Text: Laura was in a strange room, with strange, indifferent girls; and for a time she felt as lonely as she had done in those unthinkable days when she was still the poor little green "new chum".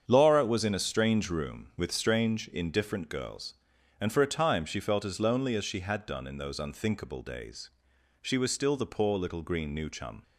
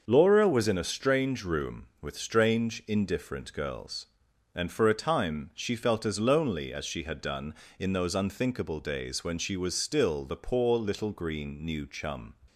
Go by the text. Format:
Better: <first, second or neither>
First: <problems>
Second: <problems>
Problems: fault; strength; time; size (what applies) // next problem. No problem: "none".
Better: second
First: starts louder than the rest; strong; until 1.0 s; 7.5 dB // skips "when"; at 7.9 s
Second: starts louder than the rest; until 1.1 s; 6.5 dB